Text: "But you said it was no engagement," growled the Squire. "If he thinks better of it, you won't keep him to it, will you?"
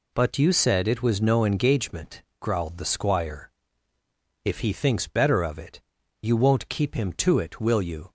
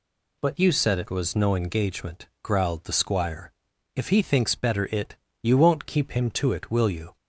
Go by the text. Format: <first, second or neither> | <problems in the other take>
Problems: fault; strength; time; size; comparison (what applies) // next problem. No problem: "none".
first | skips "of"; at 4.8 s